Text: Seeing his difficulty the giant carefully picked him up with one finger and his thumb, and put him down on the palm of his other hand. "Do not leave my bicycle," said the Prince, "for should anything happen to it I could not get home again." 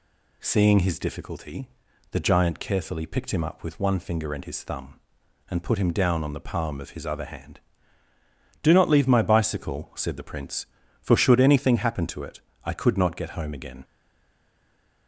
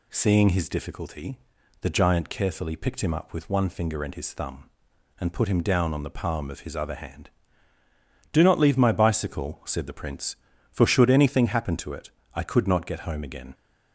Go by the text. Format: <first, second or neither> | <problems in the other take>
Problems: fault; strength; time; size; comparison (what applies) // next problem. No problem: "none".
second | pauses between "difficulty" and "the"; at 1.6 s; 0.44 s long; also in the second // pauses between "it" and "I"; slight; at 12.3 s; 0.24 s long; slight in the second // stays silent after the last word; noticeable; from 13.8 s on; 1.2 s long